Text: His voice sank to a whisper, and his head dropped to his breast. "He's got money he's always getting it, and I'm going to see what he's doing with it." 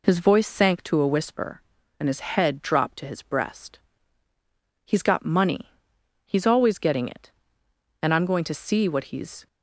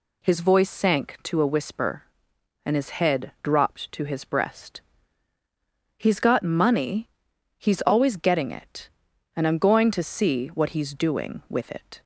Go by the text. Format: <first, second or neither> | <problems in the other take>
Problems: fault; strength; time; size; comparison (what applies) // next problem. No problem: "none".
second | pauses between "money" and "he's"; noticeable; at 5.7 s; 0.56 s long; noticeable in the second // stops before "doing with it"; at 9.4 s